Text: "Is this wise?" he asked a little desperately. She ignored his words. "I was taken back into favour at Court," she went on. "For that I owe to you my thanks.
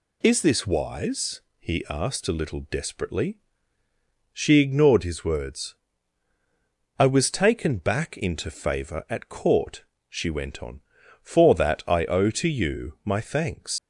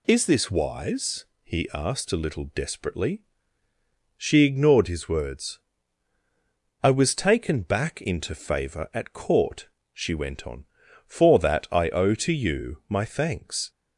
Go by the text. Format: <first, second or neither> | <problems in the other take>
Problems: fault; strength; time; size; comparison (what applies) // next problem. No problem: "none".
second | leaves "thanks" unfinished; at 13.7 s; 80 ms